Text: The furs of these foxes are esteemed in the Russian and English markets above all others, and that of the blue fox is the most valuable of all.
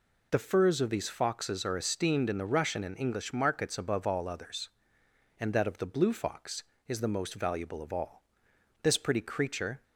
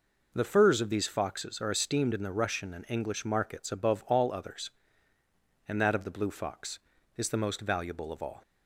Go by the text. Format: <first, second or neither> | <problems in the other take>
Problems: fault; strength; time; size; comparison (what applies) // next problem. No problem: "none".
second | goes on to say "This pretty creature"; noticeable; from 8.8 s on; 1.0 s long